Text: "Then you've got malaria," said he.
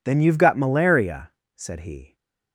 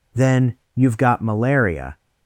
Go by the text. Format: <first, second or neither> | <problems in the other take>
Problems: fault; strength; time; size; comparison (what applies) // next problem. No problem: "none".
first | pauses between "Then" and "you've"; slight; at 0.5 s; 0.20 s long // stops before "said he"; at 1.9 s